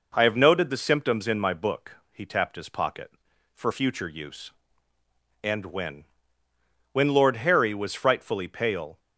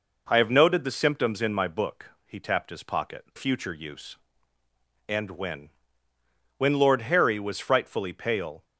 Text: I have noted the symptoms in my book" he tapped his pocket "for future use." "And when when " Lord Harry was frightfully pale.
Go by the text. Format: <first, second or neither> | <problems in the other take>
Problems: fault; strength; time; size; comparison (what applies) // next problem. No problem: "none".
first | skips "for"; at 3.3 s // pauses between "when" and "when"; noticeable; at 5.6 s; 0.88 s long; noticeable in the first